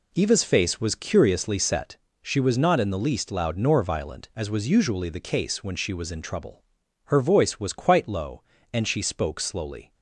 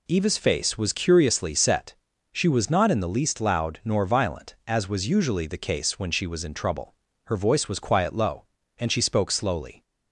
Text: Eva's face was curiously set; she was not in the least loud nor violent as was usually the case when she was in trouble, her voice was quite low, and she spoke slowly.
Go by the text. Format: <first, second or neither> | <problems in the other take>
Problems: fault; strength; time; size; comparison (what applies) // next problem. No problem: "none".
first | says "quiet" for "quite"; at 7.8 s